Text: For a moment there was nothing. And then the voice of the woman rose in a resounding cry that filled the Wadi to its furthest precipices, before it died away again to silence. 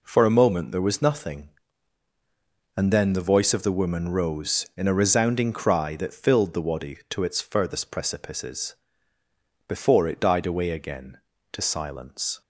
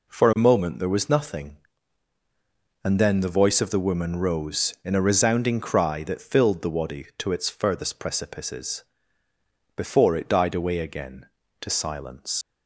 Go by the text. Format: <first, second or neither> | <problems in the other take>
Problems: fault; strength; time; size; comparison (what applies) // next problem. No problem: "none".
first | leaves "silence" unfinished; at 12.4 s; 80 ms